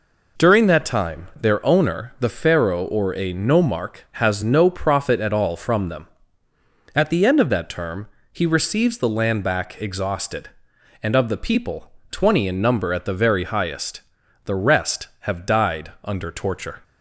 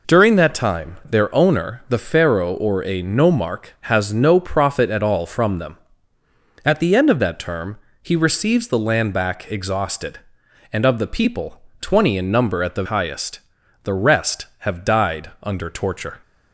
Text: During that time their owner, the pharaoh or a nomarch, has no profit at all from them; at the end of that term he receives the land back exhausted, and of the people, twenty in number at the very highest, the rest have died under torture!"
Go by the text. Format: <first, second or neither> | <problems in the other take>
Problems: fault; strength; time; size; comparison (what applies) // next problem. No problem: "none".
first | pauses between "term" and "he"; slight; at 7.7 s; 0.26 s long; slight in the first // skips "very"; at 12.8 s